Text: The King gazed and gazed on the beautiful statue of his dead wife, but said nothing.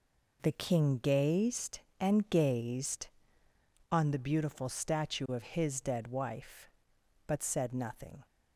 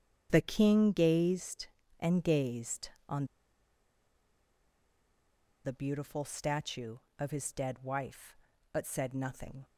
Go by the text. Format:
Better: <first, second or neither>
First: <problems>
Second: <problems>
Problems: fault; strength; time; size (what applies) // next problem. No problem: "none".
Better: first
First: none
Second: starts louder than the rest; strong; until 1.3 s; 8.5 dB // pauses between "on" and "the"; strong; at 3.2 s; 2.3 s long